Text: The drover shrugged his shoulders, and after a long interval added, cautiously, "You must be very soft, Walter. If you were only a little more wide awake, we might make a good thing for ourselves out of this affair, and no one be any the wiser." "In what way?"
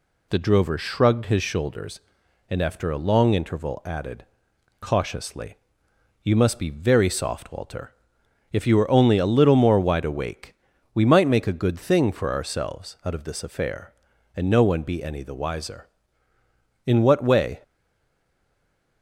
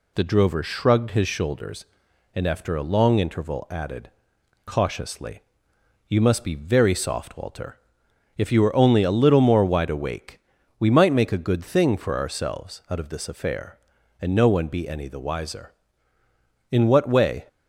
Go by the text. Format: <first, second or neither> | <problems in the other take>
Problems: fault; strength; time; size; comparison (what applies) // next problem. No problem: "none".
second | stays silent after the last word; noticeable; from 17.6 s on; 1.4 s long